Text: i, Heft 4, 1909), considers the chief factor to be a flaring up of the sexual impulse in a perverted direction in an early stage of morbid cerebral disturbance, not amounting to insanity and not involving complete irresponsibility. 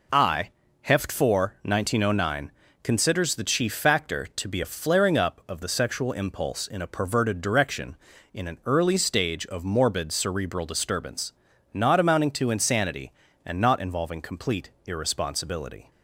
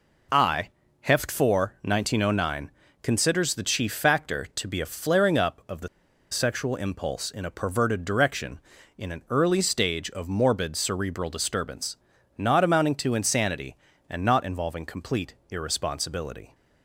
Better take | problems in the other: first | pauses between "the" and "sexual"; at 5.8 s; 0.44 s long // pauses between "complete" and "irresponsibility"; slight; at 15.3 s; 0.16 s long; slight in the first

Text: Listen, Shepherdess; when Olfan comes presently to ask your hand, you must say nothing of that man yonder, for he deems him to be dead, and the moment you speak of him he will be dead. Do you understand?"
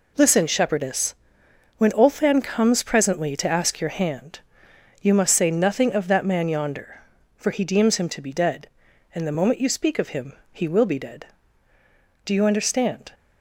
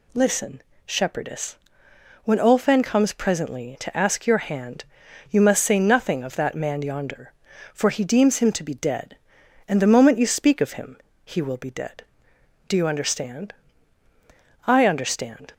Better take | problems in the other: first | pauses between "him" and "he"; slight; at 10.9 s; 0.28 s long; slight in the first // goes on to say "I understand"; noticeable; from 14.6 s on; 0.86 s long

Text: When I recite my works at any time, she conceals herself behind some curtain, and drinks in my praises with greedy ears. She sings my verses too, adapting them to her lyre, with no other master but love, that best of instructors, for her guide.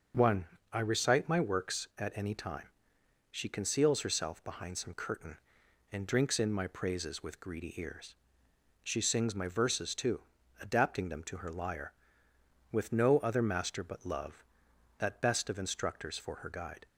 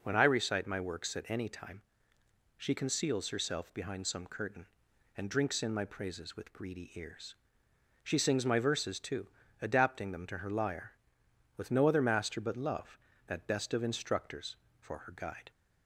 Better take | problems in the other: second | says "One" for "When"; at 0.1 s

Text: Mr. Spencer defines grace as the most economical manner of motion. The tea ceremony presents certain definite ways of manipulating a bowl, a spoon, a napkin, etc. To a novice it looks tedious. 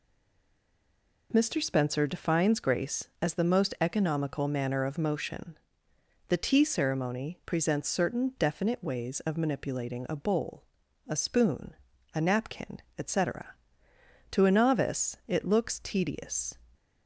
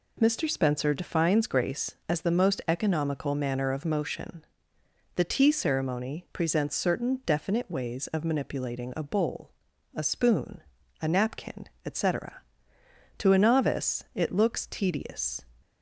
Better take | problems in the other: second | stays silent before the first word; noticeable; until 1.3 s; 1.3 s long

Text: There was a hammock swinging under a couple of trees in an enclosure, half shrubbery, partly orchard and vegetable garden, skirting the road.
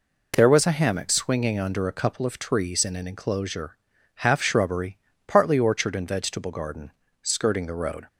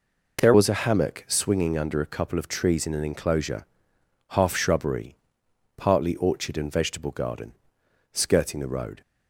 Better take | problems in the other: first | changes voice at "was"; from 0.5 s on; 8.5 s long

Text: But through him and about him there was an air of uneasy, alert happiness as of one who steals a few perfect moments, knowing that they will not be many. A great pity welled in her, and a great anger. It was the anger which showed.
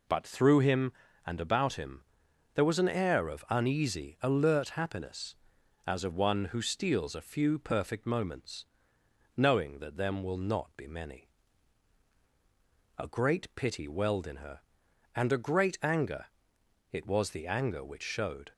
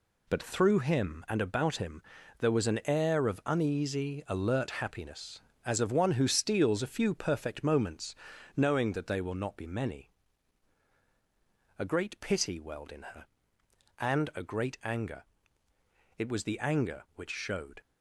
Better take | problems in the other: second | pauses between "him" and "there"; noticeable; at 2.0 s; 0.52 s long; also in the second // says "them" for "they"; at 9.9 s

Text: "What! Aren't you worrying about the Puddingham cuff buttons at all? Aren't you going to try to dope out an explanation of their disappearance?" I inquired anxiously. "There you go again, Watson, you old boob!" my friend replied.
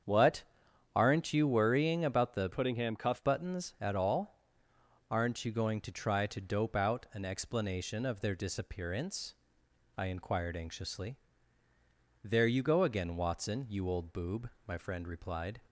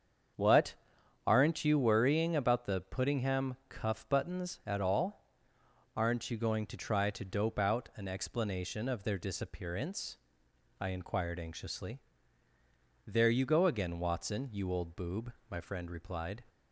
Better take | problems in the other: second | starts louder than the rest; strong; until 1.5 s; 7.5 dB; strong in the second // changes voice from "Puddingham" to "cuff"; from 2.5 to 3.2 s; 0.7 s long

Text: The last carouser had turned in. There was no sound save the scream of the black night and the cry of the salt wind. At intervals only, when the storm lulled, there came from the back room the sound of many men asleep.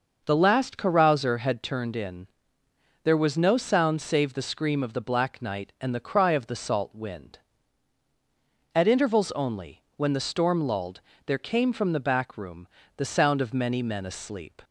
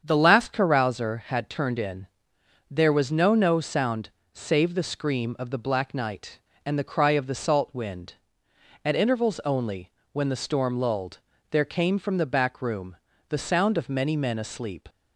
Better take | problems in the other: first | starts louder than the rest; strong; until 1.0 s; 7.5 dB // says "no" twice; at 3.3 s // pauses between "sound" and "save"; slight; at 4.0 s; 0.24 s long // pauses between "room" and "the"; slight; at 12.9 s; 0.32 s long; slight in the first

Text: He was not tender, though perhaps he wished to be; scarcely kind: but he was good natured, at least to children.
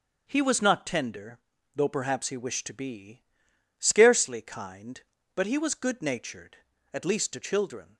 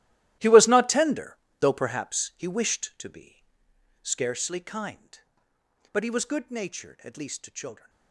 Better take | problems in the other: first | gets quieter; strong; throughout; 17 dB // starts louder than the rest; strong; until 1.6 s; 14.5 dB; also in the first

